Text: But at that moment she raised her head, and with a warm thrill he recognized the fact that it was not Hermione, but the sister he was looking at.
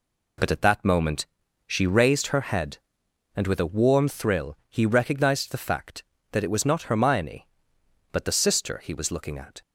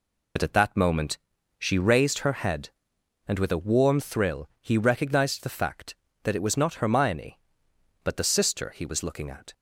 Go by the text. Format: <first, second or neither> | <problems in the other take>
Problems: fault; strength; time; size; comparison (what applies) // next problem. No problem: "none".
first | loses the start of "But"; at 0.3 s; 55 ms // pauses between "moment" and "she"; at 1.1 s; 0.42 s long; also in the first